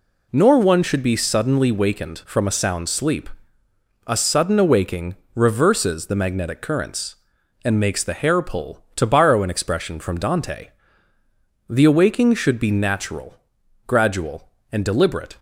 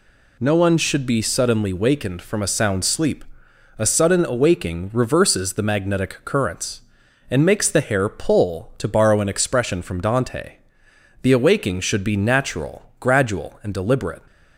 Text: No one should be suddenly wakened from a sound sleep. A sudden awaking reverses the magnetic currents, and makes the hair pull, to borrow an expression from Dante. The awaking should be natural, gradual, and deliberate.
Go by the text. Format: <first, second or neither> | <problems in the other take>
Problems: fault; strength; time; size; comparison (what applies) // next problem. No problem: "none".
second | says "Nor" for "No"; at 0.3 s // pauses between "awaking" and "reverses"; slight; at 5.1 s; 0.20 s long